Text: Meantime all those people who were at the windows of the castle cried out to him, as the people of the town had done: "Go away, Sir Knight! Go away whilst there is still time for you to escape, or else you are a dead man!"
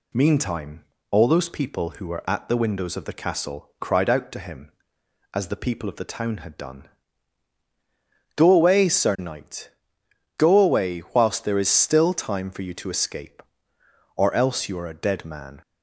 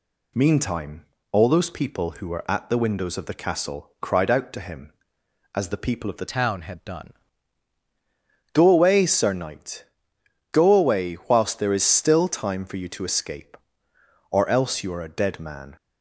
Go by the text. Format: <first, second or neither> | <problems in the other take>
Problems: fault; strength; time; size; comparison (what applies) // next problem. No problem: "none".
first | pauses between "Meantime" and "all"; slight; at 1.0 s; 0.26 s long; slight in the first // changes voice from "town" to "done"; from 6.3 to 7.1 s; 0.8 s long